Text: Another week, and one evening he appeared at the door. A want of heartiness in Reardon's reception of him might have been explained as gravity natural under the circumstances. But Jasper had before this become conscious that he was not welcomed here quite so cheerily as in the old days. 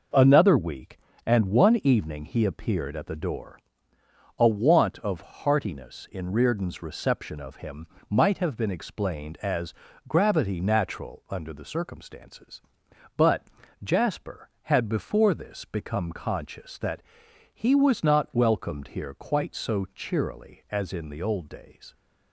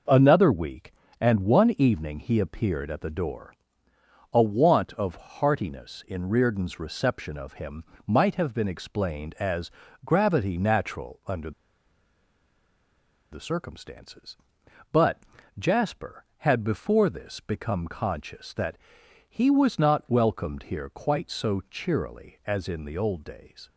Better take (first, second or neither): first